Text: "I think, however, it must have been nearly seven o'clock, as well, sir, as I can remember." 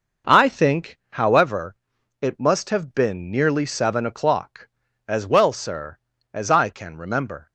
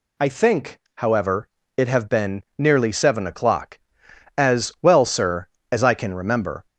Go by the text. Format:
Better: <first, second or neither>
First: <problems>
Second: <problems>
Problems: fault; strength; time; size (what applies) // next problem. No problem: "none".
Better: first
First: none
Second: skips "must"; at 1.8 s // pauses between "been" and "nearly"; slight; at 2.4 s; 0.16 s long